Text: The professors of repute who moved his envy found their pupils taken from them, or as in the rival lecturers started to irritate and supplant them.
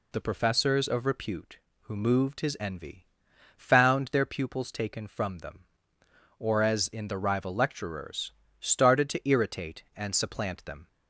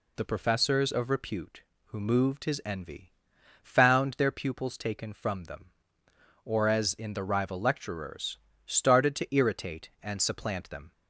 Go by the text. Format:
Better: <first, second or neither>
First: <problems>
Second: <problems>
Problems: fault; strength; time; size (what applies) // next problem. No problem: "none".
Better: neither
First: pauses between "envy" and "found"; noticeable; at 3.0 s; 0.48 s long // pauses between "lecturers" and "started"; slight; at 8.3 s; 0.28 s long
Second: pauses between "envy" and "found"; noticeable; at 3.1 s; 0.48 s long // pauses between "lecturers" and "started"; slight; at 8.3 s; 0.28 s long